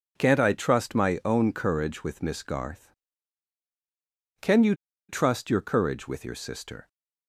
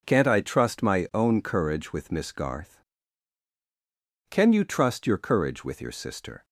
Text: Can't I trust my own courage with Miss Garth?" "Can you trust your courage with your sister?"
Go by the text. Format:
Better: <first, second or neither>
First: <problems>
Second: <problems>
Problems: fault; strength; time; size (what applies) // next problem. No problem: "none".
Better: second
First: pauses between "you" and "trust"; slight; at 4.7 s; 0.35 s long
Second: none